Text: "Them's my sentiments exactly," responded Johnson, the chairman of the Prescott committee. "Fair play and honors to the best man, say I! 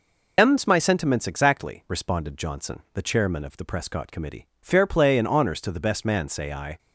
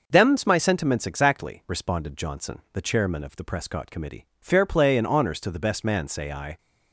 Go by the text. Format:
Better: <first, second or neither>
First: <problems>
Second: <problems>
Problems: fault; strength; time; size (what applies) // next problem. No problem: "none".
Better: second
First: loses the start of "Them's"; at 0.3 s; 105 ms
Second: none